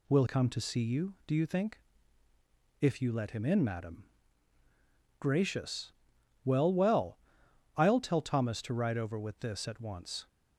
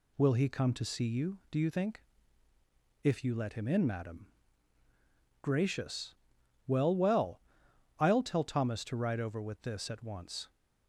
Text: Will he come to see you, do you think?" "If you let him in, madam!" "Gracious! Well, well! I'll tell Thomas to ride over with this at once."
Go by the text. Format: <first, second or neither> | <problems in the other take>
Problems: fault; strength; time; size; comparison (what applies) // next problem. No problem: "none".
second | skips "he"; at 0.2 s